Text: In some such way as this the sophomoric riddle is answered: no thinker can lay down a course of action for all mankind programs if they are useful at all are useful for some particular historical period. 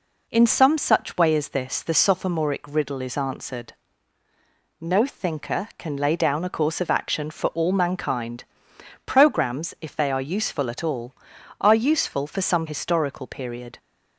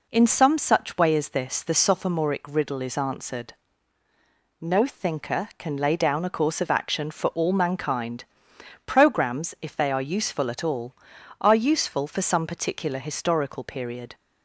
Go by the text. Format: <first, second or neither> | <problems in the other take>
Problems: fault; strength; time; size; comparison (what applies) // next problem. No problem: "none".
second | pauses between "mankind" and "programs"; noticeable; at 8.4 s; 0.62 s long; noticeable in the second // skips "particular"; at 12.6 s